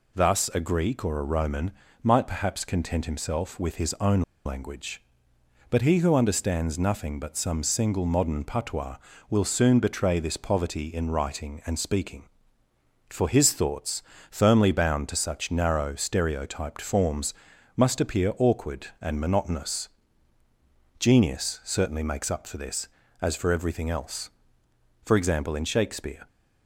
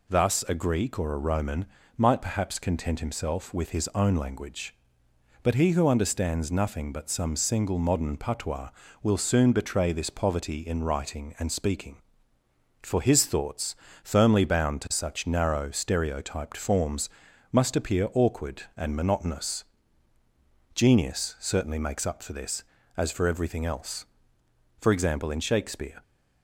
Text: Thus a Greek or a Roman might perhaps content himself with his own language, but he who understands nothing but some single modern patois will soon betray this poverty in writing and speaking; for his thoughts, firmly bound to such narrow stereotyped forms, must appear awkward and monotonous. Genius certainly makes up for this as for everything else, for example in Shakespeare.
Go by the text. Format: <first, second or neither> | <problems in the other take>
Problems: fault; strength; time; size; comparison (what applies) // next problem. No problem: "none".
second | pauses between "Roman" and "might"; slight; at 1.7 s; 0.32 s long; slight in the second // pauses between "own" and "language"; slight; at 4.2 s; 0.24 s long